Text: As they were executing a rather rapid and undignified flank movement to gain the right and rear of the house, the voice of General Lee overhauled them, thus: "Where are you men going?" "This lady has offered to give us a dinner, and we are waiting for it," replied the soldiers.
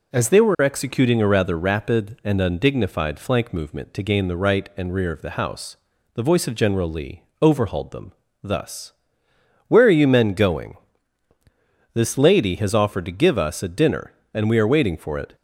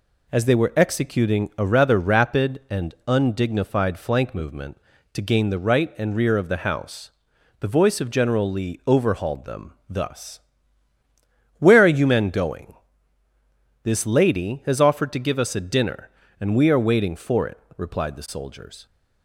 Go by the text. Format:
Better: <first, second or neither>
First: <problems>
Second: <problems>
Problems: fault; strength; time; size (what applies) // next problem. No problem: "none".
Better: second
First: pauses between "Lee" and "overhauled"; slight; at 7.2 s; 0.18 s long // stops before "replied the soldiers"; at 15.3 s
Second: none